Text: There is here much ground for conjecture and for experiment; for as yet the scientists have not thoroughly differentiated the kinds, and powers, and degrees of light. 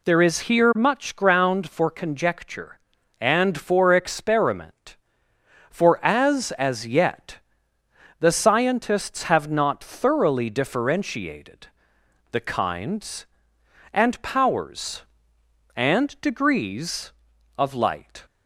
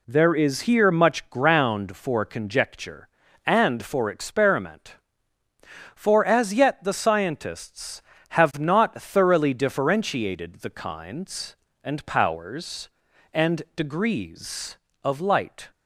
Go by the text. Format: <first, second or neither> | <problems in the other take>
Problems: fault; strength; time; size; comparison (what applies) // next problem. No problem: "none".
second | says "as" twice; at 6.5 s // pauses between "yet" and "the"; noticeable; at 7.3 s; 0.82 s long // pauses between "differentiated" and "the"; noticeable; at 11.6 s; 0.66 s long